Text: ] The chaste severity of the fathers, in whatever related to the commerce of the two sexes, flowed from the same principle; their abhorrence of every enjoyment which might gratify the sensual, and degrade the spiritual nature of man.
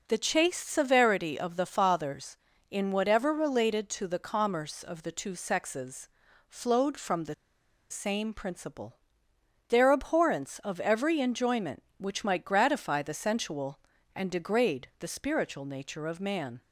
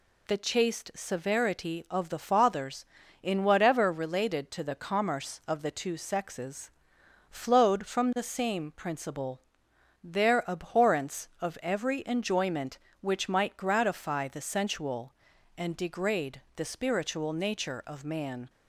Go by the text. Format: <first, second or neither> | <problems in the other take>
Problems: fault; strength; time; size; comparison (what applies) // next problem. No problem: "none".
second | pauses between "the" and "same"; noticeable; at 7.3 s; 0.57 s long